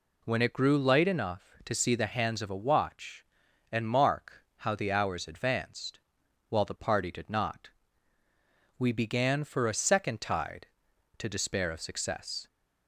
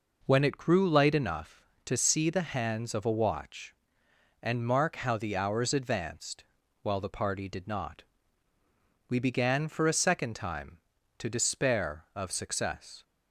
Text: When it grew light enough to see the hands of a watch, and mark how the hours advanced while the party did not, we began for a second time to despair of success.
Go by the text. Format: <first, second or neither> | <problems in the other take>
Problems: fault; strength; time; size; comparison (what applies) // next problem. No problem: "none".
second | pauses between "advanced" and "while"; noticeable; at 5.9 s; 0.50 s long; also in the second // says "tide" for "time"; at 10.2 s